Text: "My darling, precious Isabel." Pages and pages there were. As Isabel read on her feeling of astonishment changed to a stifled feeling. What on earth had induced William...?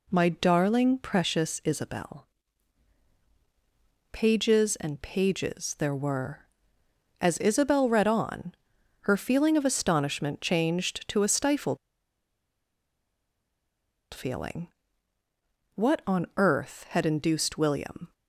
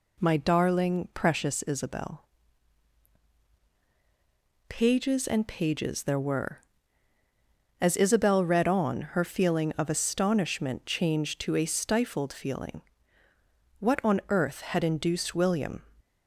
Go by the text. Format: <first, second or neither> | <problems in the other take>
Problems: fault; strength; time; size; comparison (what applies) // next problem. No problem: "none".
second | pauses between "on" and "her"; noticeable; at 8.5 s; 0.48 s long // pauses between "stifled" and "feeling"; strong; at 11.7 s; 2.3 s long